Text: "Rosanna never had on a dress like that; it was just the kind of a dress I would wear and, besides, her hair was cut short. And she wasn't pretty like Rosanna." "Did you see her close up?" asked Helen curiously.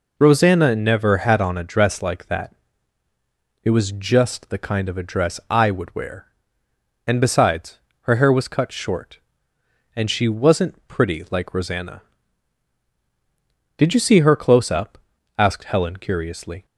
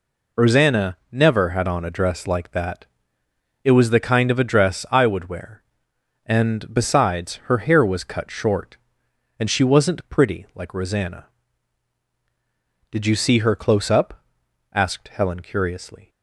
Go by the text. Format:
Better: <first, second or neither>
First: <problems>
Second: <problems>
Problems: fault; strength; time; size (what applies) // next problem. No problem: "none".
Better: first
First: none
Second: skips "just"; at 3.8 s